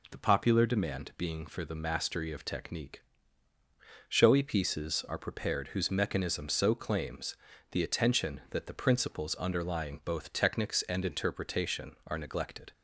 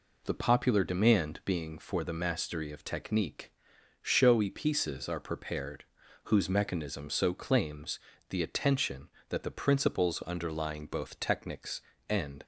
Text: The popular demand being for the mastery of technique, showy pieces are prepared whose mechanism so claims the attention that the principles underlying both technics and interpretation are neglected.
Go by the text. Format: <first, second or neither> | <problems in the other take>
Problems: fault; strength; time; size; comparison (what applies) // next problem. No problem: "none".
first | pauses between "prepared" and "whose"; at 5.8 s; 0.42 s long // pauses between "claims" and "the"; slight; at 7.9 s; 0.32 s long; slight in the first // stops before "interpretation are neglected"; at 12.4 s